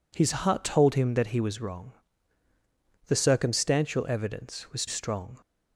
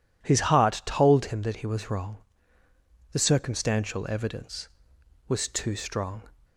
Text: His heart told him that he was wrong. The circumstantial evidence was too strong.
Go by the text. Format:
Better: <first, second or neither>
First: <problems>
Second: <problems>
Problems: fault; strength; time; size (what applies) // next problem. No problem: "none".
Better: second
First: skips "too"; at 4.8 s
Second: none